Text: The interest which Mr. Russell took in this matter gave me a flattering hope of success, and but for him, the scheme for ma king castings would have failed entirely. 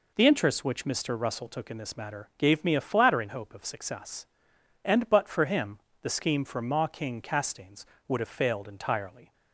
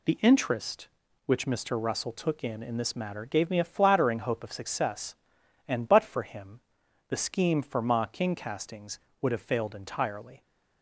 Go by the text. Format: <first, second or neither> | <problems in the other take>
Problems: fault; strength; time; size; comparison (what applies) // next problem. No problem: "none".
first | says "in" twice; at 2.6 s